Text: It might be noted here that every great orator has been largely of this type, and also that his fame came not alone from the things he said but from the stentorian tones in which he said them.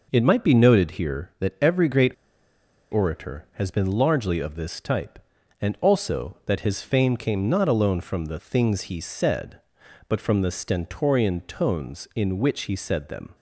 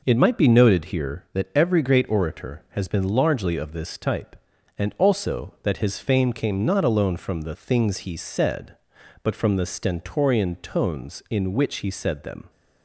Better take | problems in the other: second | pauses between "great" and "orator"; noticeable; at 2.1 s; 0.79 s long

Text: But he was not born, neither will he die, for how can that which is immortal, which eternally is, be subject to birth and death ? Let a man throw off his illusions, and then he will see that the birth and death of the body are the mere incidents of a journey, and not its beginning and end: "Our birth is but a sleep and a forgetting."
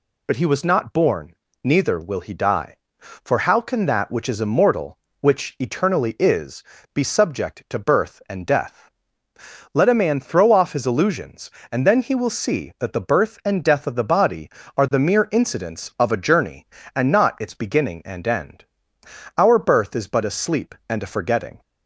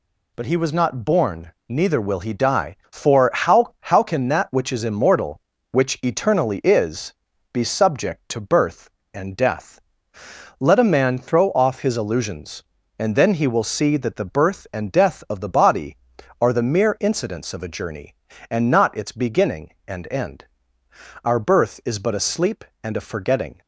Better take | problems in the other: first | says "how" twice; at 3.7 s

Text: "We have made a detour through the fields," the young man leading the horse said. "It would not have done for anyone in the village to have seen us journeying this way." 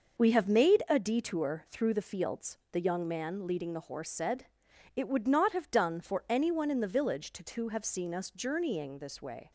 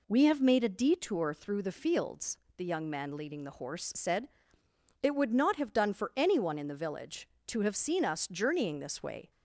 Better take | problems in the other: second | says "to" twice; at 7.4 s

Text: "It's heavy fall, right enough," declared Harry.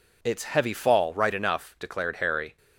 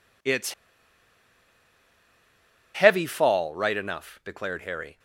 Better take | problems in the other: first | pauses between "It's" and "heavy"; strong; at 0.5 s; 2.2 s long

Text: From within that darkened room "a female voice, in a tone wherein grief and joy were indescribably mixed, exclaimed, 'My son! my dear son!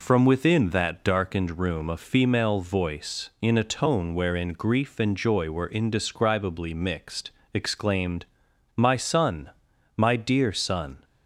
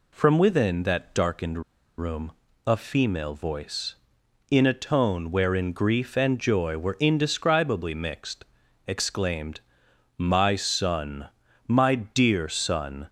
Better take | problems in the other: first | pauses between "darkened" and "room"; at 1.6 s; 0.37 s long // pauses between "room" and "a"; slight; at 2.3 s; 0.34 s long

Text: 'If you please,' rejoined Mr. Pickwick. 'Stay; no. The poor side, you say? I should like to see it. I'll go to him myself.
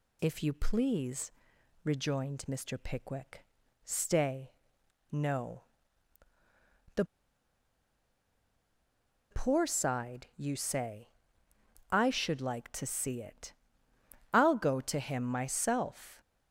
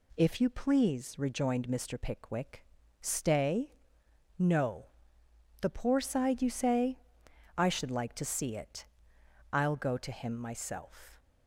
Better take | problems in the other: second | pauses between "The" and "poor"; strong; at 7.0 s; 2.2 s long

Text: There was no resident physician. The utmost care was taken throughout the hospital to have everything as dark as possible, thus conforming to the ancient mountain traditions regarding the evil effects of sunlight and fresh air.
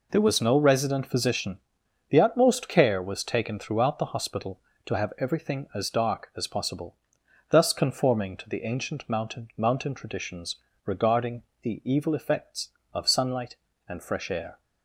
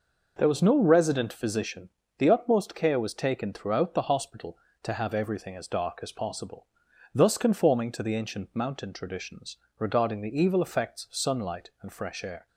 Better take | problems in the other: second | says "mountain" twice; at 9.5 s // pauses between "traditions" and "regarding"; slight; at 10.5 s; 0.30 s long; slight in the second // pauses between "regarding" and "the"; slight; at 11.4 s; 0.18 s long

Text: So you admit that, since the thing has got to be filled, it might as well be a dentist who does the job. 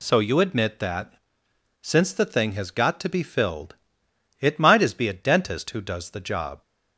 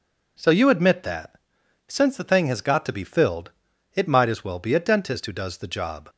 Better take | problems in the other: second | skips "well"; at 4.9 s

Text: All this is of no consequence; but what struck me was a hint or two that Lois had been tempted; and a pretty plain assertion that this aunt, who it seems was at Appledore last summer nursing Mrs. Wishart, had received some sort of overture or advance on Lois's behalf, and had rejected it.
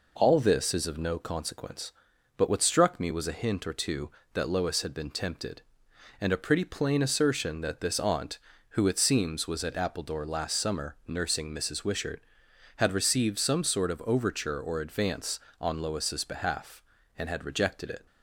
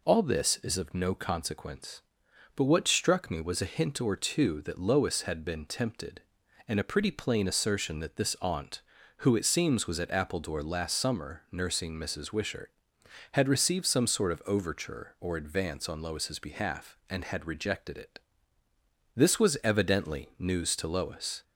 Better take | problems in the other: first | goes on to say "This was evidently news to Lois"; strong; from 19.1 s on; 2.2 s long

